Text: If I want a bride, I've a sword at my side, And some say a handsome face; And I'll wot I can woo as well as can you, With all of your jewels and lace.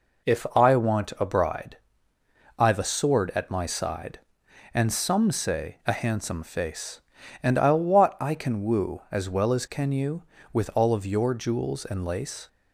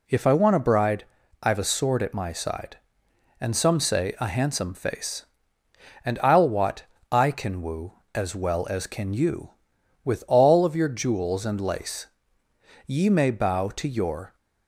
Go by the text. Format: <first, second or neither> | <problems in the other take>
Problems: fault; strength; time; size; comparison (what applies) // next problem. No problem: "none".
first | pauses between "wot" and "I"; slight; at 6.8 s; 0.27 s long // goes on to say "Ye may bow to your"; from 12.8 s on; 1.5 s long